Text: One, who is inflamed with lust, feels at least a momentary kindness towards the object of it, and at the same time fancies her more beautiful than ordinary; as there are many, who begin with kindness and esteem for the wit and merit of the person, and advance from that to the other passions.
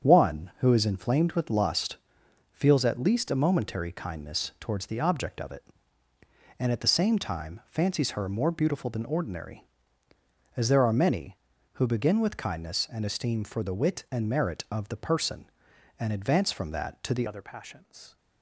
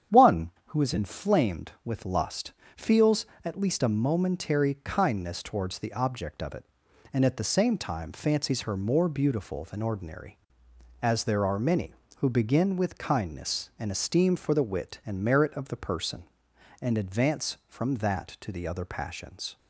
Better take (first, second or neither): second